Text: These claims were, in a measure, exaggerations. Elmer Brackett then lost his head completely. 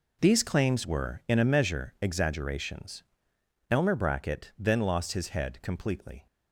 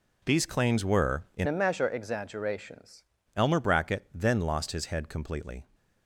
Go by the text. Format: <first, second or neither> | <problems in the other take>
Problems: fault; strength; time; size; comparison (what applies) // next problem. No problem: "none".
first | changes voice from "a" to "exaggerations"; from 1.4 to 3.0 s; 1.6 s long